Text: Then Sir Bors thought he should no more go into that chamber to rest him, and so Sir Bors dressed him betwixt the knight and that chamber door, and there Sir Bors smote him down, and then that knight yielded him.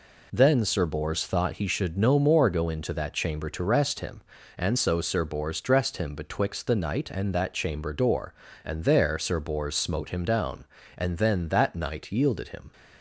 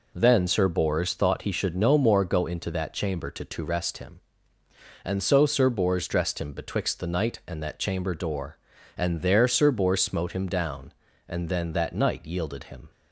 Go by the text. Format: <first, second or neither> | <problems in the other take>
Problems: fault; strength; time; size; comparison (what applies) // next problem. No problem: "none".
first | says "to" twice; at 3.4 s